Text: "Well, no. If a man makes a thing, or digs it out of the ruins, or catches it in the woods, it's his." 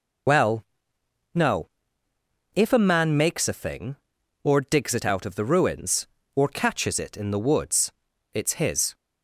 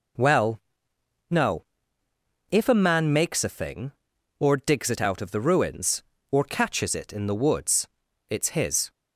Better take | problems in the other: second | loses the start of "Well"; at 0.2 s; 65 ms

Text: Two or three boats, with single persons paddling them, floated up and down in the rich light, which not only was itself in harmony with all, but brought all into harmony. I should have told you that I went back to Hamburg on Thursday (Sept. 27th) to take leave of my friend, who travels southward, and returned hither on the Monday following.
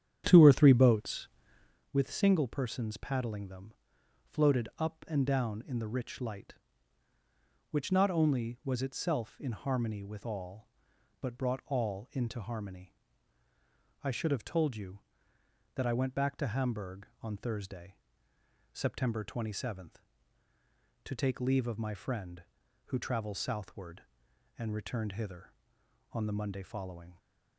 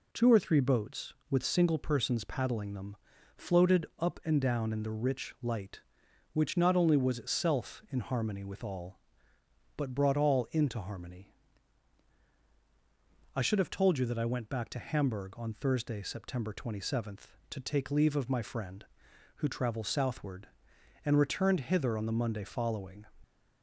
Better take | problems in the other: second | starts louder than the rest; strong; until 1.9 s; 9 dB

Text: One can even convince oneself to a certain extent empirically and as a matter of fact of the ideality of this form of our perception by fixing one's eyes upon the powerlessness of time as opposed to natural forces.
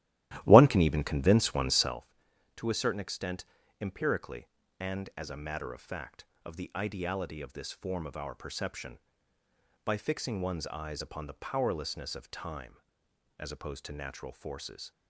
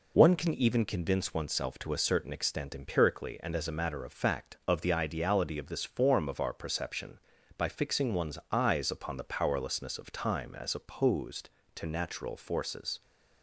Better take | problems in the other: second | starts louder than the rest; strong; until 1.9 s; 14.5 dB // pauses between "extent" and "empirically"; at 3.4 s; 0.38 s long

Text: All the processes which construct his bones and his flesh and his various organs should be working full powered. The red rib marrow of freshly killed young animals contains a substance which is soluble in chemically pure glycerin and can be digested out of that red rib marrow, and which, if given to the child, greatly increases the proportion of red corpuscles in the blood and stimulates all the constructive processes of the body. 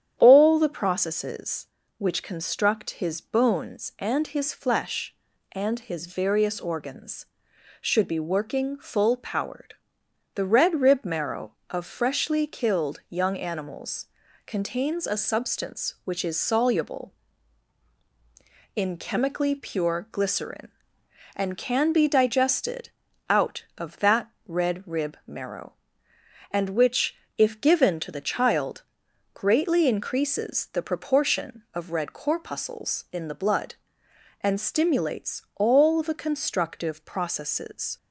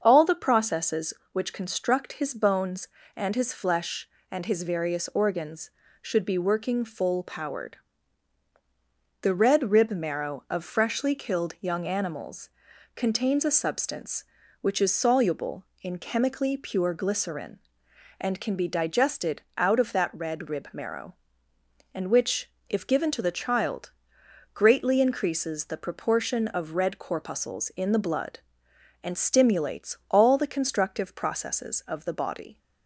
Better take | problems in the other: second | starts louder than the rest; strong; until 1.1 s; 9.5 dB; also in the second // pauses between "animals" and "contains"; at 14.0 s; 0.38 s long; noticeable in the second // pauses between "digested" and "out"; at 22.8 s; 0.40 s long // pauses between "that" and "red"; slight; at 24.2 s; 0.18 s long // stops before "of the body"; at 37.9 s

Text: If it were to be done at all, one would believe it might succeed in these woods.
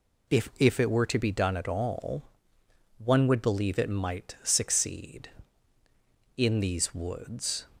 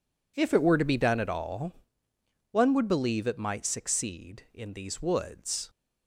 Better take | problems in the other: second | says "If" twice; at 0.5 s

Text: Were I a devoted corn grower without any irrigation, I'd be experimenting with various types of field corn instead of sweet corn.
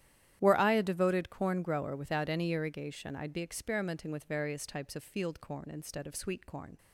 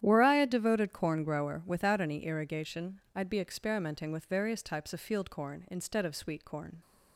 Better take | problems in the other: neither | starts louder than the rest; strong; the same in both

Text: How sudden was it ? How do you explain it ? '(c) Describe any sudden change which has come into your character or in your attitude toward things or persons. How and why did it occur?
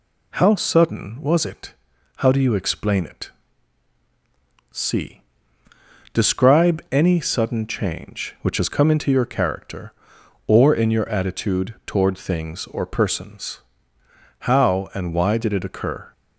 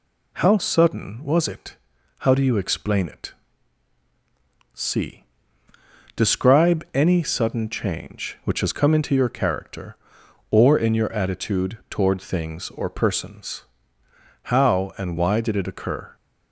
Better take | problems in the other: neither | none

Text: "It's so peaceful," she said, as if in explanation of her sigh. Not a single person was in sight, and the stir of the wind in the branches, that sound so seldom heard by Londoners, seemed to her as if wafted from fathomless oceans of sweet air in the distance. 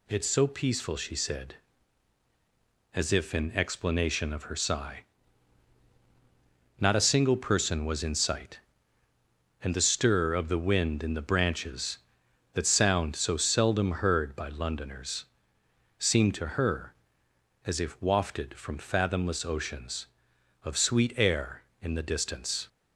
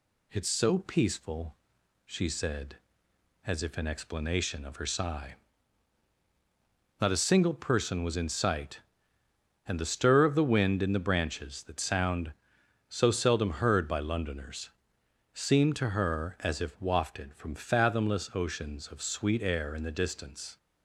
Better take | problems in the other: neither | none

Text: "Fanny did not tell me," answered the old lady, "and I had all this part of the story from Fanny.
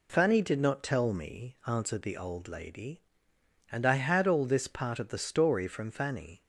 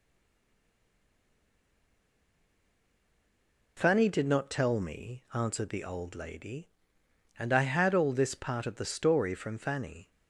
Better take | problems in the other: first | stays silent before the first word; strong; until 3.7 s; 3.7 s long

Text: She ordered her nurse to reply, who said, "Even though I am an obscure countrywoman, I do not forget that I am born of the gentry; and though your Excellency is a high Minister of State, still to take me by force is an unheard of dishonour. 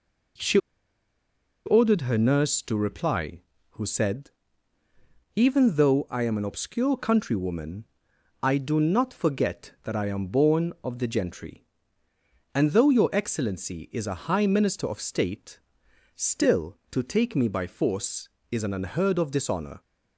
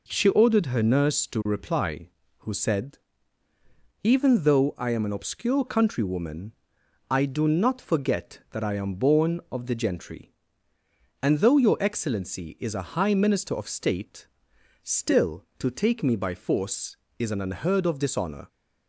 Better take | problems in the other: second | pauses between "She" and "ordered"; at 0.5 s; 1.0 s long

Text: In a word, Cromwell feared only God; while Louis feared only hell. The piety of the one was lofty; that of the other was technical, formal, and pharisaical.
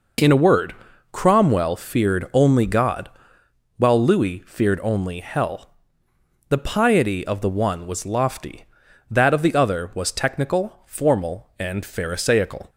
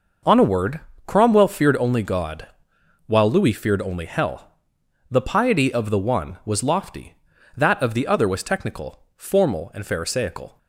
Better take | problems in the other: first | says "On" for "In"; at 0.2 s

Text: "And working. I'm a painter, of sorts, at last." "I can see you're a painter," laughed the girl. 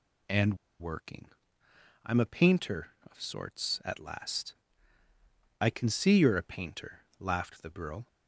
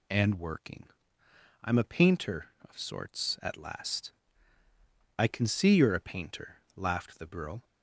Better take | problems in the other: second | pauses between "And" and "working"; slight; at 0.5 s; 0.25 s long

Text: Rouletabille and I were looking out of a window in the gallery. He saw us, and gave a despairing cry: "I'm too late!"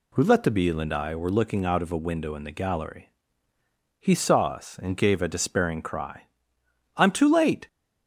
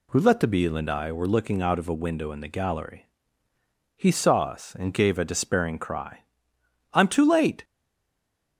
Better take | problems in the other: first | stays silent after the last word; slight; from 7.6 s on; 0.9 s long

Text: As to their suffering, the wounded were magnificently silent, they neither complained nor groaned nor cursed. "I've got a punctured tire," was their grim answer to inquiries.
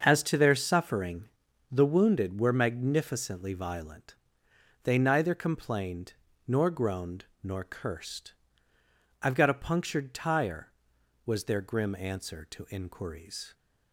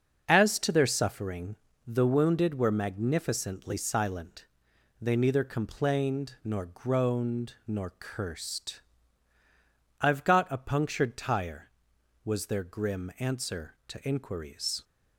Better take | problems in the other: second | starts louder than the rest; until 1.0 s; 6.5 dB; also in the second // says "violent" for "silent"; at 3.5 s // pauses between "complained" and "nor"; slight; at 6.1 s; 0.34 s long // pauses between "groaned" and "nor"; slight; at 7.2 s; 0.18 s long

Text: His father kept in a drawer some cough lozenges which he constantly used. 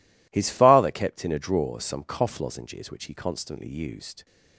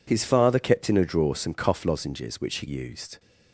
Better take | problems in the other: first | skips "constantly"; at 2.6 s

